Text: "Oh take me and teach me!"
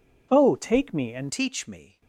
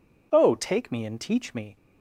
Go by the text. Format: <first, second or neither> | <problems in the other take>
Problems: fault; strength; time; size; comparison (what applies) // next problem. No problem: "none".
second | changes voice at "teach"; from 1.3 s on; 0.7 s long